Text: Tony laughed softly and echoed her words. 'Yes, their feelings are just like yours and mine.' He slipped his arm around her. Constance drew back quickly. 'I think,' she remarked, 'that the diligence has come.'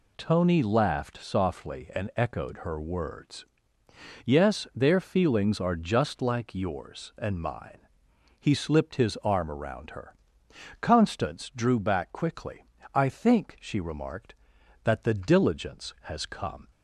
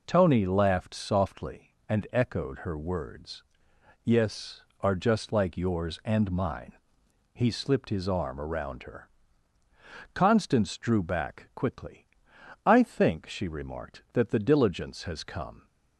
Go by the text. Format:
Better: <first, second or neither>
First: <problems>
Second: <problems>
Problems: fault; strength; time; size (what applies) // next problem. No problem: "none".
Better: first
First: none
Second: skips "their feelings"; at 4.7 s